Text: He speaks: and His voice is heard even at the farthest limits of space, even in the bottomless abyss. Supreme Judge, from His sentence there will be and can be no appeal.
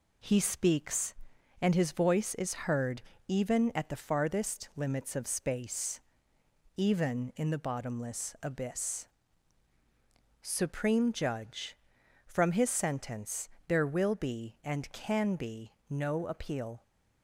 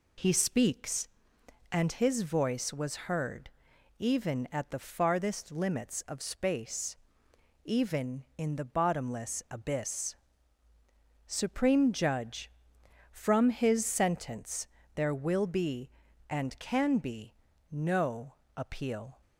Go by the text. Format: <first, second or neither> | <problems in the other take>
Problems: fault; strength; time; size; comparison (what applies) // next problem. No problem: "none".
first | says "was" for "is"; at 2.7 s // pauses between "heard" and "even"; noticeable; at 3.5 s; 0.48 s long; slight in the first // pauses between "sentence" and "there"; slight; at 14.6 s; 0.28 s long; slight in the first // pauses between "be" and "no"; at 17.3 s; 0.38 s long; slight in the first // pauses between "no" and "appeal"; slight; at 18.3 s; 0.24 s long